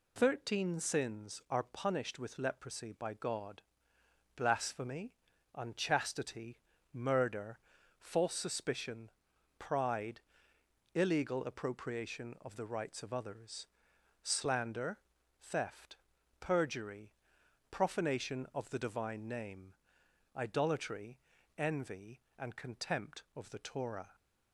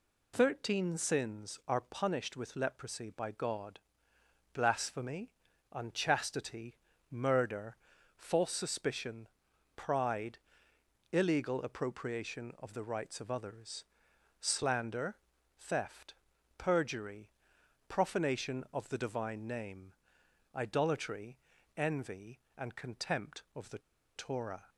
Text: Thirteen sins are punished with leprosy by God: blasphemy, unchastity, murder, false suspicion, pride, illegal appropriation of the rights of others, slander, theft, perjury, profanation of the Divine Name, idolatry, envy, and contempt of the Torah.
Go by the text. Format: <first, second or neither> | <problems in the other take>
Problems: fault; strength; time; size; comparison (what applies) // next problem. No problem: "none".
first | pauses between "the" and "Torah"; at 23.7 s; 0.37 s long